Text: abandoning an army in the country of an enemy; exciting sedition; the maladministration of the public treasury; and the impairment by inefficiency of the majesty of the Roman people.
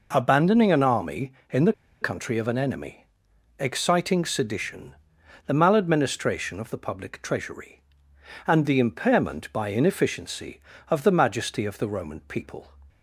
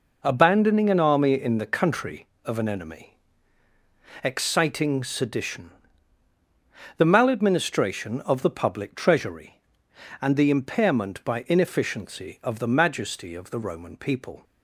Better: second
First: pauses between "the" and "country"; slight; at 1.7 s; 0.27 s long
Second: none

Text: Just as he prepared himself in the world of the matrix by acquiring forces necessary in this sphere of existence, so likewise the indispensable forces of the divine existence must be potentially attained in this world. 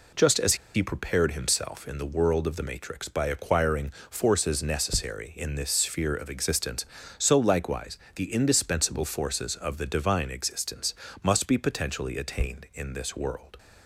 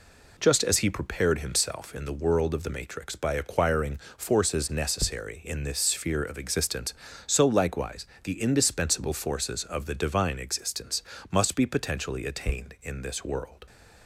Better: second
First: pauses between "as" and "he"; slight; at 0.5 s; 0.20 s long // pauses between "acquiring" and "forces"; slight; at 3.9 s; 0.18 s long // pauses between "likewise" and "the"; slight; at 7.9 s; 0.16 s long // pauses between "existence" and "must"; slight; at 10.9 s; 0.30 s long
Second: pauses between "acquiring" and "forces"; slight; at 3.9 s; 0.18 s long // pauses between "likewise" and "the"; slight; at 8.0 s; 0.16 s long // pauses between "existence" and "must"; slight; at 11.0 s; 0.30 s long

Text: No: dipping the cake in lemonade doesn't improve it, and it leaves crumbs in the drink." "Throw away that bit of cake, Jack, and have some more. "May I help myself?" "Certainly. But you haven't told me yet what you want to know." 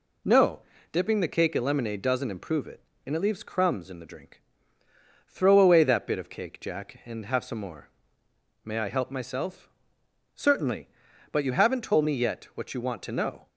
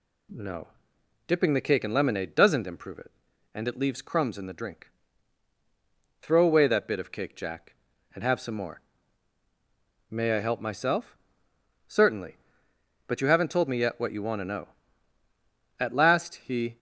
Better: first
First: none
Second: goes on to say "At last he"; noticeable; from 15.7 s on; 0.98 s long

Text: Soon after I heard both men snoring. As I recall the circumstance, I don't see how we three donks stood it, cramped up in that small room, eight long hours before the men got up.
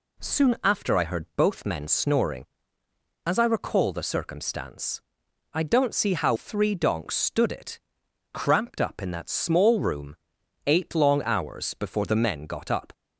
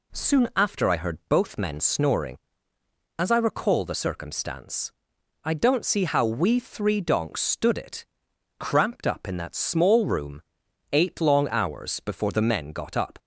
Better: second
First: skips "we"; at 6.3 s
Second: none

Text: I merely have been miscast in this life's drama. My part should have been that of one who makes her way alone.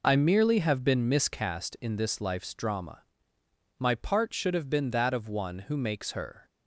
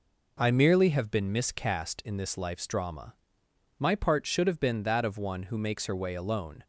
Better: second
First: stops before "way alone"; at 6.4 s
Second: none

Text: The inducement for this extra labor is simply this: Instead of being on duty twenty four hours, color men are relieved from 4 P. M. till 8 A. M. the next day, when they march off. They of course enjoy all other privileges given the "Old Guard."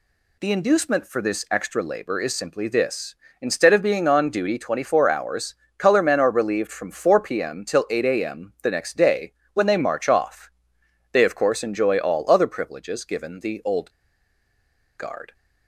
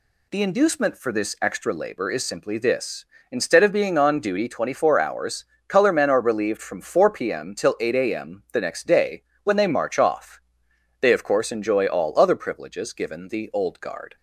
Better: second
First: pauses between "Old" and "Guard"; at 13.8 s; 1.0 s long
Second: none

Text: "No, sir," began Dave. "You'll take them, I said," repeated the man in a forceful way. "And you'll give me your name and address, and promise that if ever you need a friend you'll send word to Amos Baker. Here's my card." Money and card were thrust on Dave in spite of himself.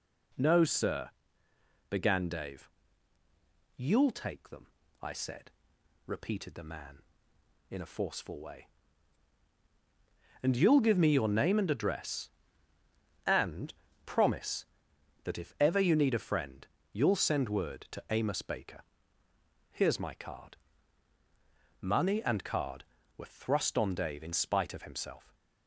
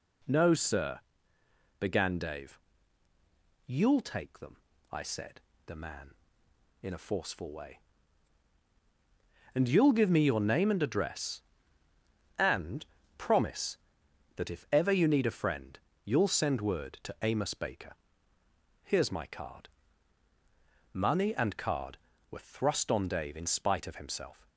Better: first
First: pauses between "and" and "promise"; slight; at 13.7 s; 0.32 s long // pauses between "friend" and "you'll"; slight; at 16.6 s; 0.26 s long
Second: skips "repeated"; at 5.5 s // pauses between "and" and "promise"; slight; at 12.8 s; 0.32 s long // pauses between "friend" and "you'll"; slight; at 15.7 s; 0.26 s long

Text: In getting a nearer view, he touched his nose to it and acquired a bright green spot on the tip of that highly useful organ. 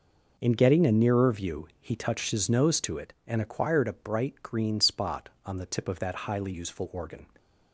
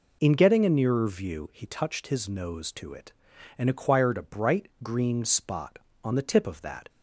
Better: first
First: none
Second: stops before "highly useful organ"; at 6.8 s

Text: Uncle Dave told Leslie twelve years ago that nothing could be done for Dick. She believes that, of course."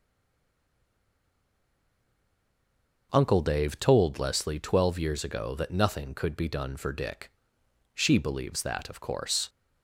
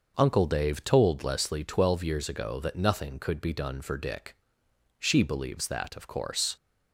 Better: second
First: stays silent before the first word; strong; until 3.1 s; 3.1 s long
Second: none

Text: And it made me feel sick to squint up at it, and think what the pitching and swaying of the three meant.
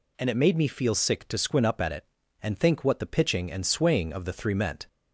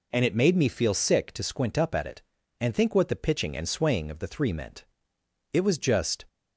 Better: first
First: none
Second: goes on to say "It was just"; noticeable; from 5.5 s on; 0.72 s long

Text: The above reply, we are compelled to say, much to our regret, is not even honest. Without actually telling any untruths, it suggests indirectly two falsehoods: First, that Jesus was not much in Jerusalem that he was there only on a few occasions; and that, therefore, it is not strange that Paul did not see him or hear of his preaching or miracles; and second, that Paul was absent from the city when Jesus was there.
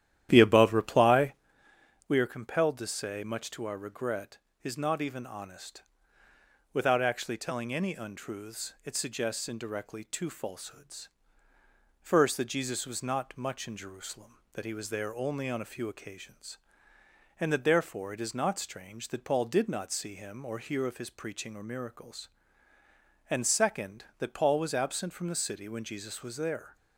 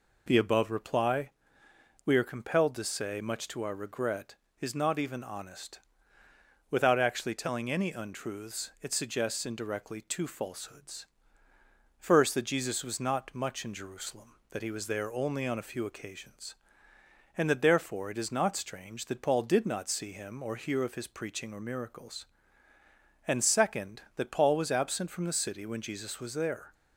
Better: second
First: starts louder than the rest; strong; until 1.5 s; 11.5 dB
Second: none

